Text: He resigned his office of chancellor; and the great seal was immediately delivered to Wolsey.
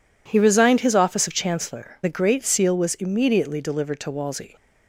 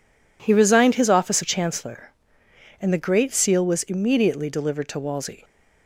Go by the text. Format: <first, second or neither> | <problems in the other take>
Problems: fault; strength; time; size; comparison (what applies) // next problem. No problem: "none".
second | skips "and"; at 2.0 s